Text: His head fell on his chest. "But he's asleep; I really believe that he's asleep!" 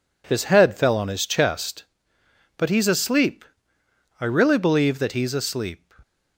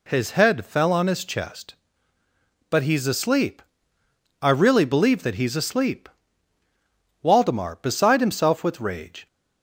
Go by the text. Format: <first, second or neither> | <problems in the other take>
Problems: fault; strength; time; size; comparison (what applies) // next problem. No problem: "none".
first | goes on to say "Waldemar beside himself with rage"; strong; from 7.2 s on; 2.0 s long